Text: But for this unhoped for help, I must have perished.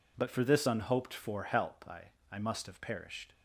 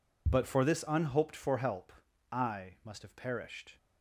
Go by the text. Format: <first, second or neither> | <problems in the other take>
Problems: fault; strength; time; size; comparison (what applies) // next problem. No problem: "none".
second | says "I" twice; at 2.3 s